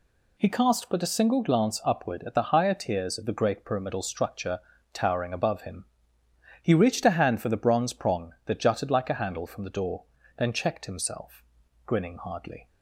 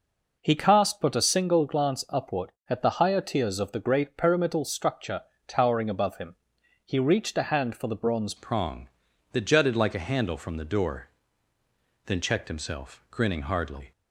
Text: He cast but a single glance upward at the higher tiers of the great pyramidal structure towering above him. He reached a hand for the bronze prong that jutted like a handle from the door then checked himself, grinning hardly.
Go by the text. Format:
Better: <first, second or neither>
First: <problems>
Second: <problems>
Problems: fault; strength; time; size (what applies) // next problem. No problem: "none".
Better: first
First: pauses between "structure" and "towering"; slight; at 4.5 s; 0.34 s long // pauses between "door" and "then"; slight; at 10.0 s; 0.34 s long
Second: pauses between "structure" and "towering"; slight; at 5.2 s; 0.24 s long // changes voice at "prong"; from 8.3 s on; 5.6 s long // pauses between "door" and "then"; noticeable; at 11.0 s; 0.98 s long